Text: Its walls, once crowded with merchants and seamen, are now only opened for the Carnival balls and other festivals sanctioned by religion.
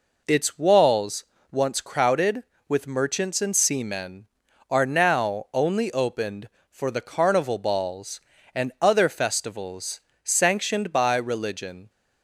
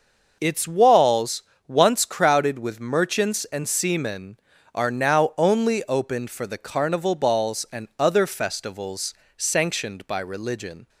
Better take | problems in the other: neither | pauses between "festivals" and "sanctioned"; slight; the same in both

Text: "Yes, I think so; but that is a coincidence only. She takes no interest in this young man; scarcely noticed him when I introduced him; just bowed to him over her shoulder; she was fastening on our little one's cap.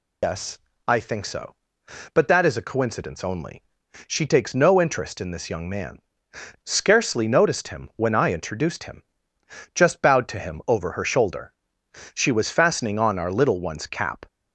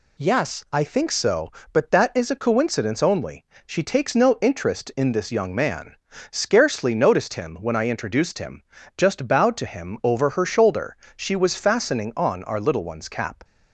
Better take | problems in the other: second | loses the start of "Yes"; at 0.2 s; 105 ms

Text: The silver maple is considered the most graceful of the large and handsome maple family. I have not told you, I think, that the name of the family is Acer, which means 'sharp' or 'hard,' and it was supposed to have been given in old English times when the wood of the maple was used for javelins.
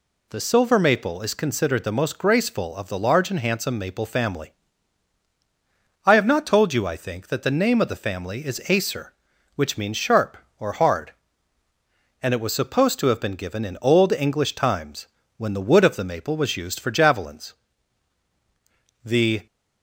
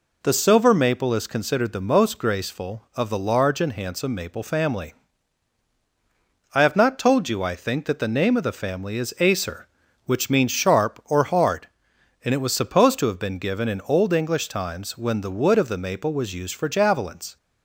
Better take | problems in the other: second | pauses between "times" and "when"; slight; at 15.0 s; 0.30 s long // goes on to say "The"; slight; from 19.0 s on; 0.42 s long

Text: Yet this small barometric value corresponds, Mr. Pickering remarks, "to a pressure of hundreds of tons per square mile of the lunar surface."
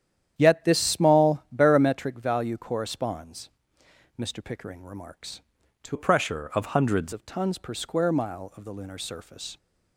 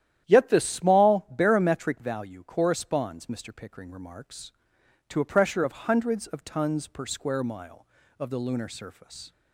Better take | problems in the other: second | starts louder than the rest; strong; until 1.3 s; 10 dB; strong in the second // changes voice from "a" to "hundreds"; from 5.9 to 7.1 s; 1.2 s long

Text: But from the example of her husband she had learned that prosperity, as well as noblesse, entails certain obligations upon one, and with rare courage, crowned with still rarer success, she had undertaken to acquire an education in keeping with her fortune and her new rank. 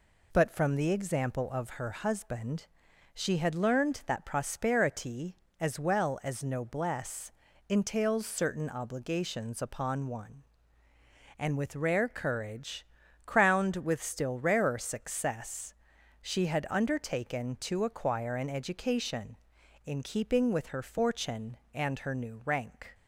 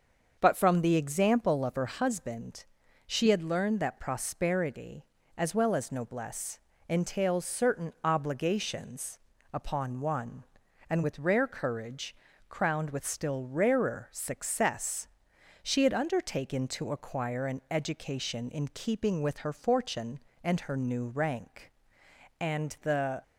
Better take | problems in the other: first | starts louder than the rest; until 1.4 s; 6.5 dB // pauses between "husband" and "she"; at 2.6 s; 0.44 s long; noticeable in the first // pauses between "obligations" and "upon"; slight; at 9.1 s; 0.34 s long // goes on to say "And the"; noticeable; from 22.4 s on; 0.82 s long

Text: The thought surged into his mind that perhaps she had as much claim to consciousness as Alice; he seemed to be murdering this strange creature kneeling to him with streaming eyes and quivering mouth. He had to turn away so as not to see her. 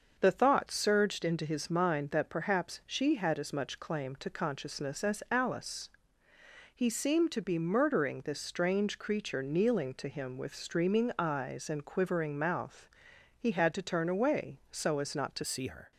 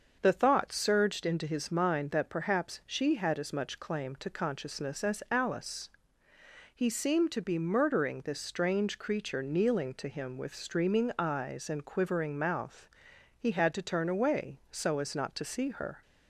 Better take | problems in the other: second | starts louder than the rest; until 1.2 s; 6.5 dB; also in the second // changes voice at "see"; from 15.4 s on; 0.5 s long

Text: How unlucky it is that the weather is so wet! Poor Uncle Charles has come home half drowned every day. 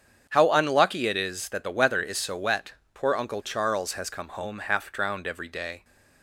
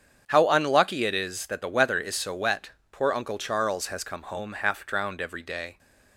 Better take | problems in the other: neither | starts louder than the rest; strong; the same in both

